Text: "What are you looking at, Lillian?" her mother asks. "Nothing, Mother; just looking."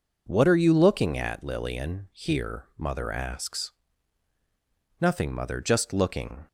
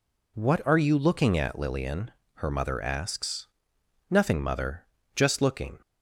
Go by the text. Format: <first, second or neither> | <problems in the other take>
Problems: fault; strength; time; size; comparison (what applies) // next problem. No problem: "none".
second | says "here" for "her"; at 2.1 s